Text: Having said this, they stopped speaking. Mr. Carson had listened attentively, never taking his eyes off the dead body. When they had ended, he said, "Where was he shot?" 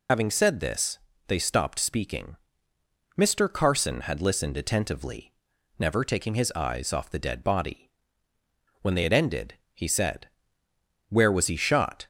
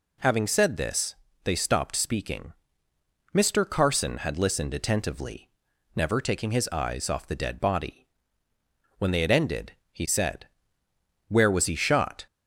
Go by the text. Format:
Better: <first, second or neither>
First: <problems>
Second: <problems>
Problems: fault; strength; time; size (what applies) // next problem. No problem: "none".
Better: second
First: loses the start of "Having"; at 0.0 s; 75 ms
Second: none